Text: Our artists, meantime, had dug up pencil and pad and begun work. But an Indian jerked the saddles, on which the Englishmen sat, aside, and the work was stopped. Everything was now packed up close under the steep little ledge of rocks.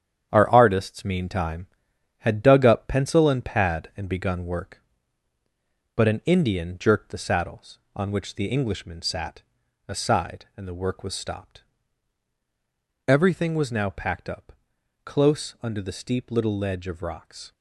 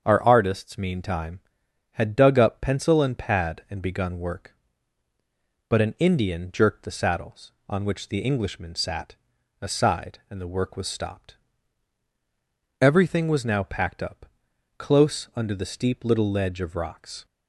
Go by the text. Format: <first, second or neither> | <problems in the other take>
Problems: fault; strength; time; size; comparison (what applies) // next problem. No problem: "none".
second | gets quieter; strong; throughout; 7 dB // starts louder than the rest; strong; until 1.3 s; 9 dB; strong in the second // pauses between "up" and "close"; noticeable; at 14.5 s; 0.54 s long; noticeable in the second